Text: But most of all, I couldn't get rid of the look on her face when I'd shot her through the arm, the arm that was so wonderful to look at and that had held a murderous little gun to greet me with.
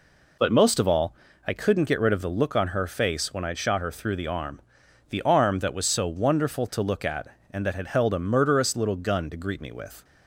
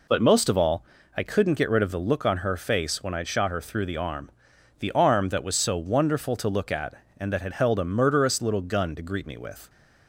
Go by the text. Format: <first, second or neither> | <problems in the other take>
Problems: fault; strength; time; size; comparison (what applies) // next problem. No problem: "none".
neither | none